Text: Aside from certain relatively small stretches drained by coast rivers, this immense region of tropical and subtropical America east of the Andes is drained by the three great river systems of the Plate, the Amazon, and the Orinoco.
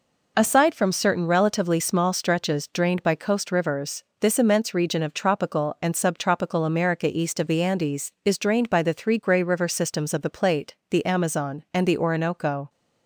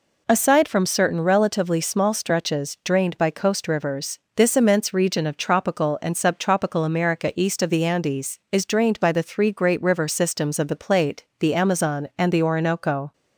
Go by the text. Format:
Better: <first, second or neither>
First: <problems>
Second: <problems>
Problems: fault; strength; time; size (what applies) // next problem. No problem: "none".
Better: second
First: says "grey" for "great"; at 9.1 s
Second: none